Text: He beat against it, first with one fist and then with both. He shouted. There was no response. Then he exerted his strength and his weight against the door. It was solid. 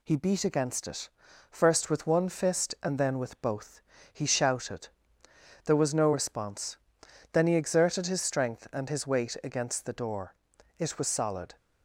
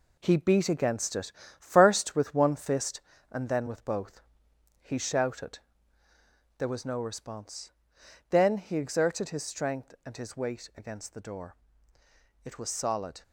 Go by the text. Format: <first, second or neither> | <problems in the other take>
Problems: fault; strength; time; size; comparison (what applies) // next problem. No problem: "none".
first | gets quieter; throughout; 6.5 dB